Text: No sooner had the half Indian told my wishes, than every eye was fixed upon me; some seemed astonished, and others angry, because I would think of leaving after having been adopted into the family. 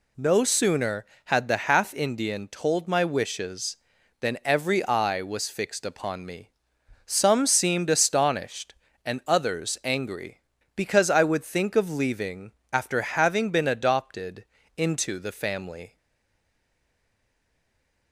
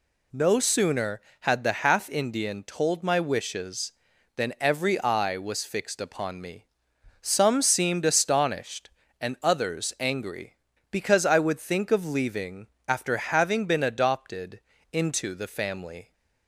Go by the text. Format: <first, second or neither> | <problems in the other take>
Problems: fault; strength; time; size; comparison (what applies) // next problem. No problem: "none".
second | pauses between "leaving" and "after"; slight; at 12.5 s; 0.18 s long; slight in the second // pauses between "adopted" and "into"; slight; at 14.4 s; 0.32 s long; slight in the second // stays silent after the last word; from 15.9 s on; 2.2 s long